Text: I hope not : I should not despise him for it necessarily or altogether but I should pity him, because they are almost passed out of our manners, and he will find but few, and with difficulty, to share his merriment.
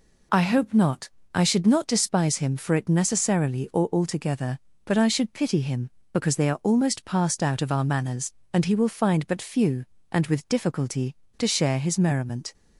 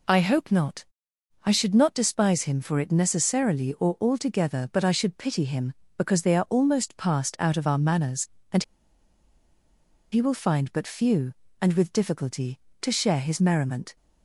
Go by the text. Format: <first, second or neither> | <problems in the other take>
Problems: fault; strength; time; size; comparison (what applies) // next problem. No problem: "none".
first | pauses between "and" and "he"; strong; at 8.6 s; 1.4 s long